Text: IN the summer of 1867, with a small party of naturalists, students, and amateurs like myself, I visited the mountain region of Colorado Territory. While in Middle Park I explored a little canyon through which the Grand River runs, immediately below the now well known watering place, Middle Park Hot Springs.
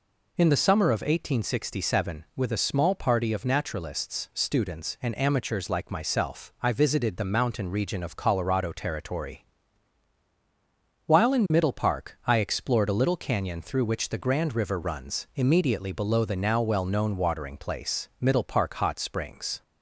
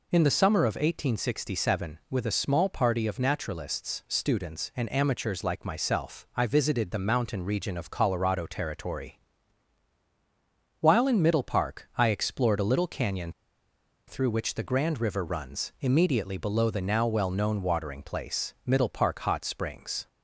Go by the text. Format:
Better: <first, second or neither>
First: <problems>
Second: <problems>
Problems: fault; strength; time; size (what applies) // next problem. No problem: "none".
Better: first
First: none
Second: pauses between "canyon" and "through"; noticeable; at 13.3 s; 0.74 s long